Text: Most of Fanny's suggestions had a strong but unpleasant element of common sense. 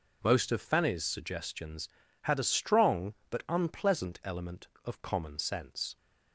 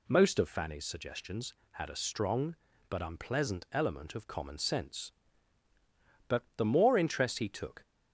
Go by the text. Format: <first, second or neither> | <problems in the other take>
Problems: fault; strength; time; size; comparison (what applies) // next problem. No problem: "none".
first | goes on to say "But the more interest he took"; from 6.2 s on; 1.5 s long